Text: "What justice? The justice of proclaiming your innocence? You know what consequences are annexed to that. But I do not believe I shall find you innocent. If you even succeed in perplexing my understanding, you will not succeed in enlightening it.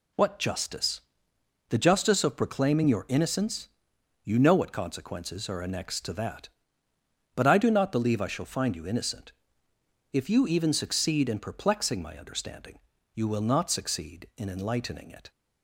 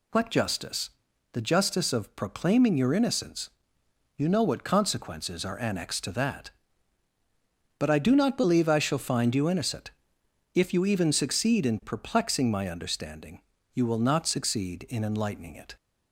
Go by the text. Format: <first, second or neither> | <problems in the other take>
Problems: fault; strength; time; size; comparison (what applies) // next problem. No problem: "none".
neither | none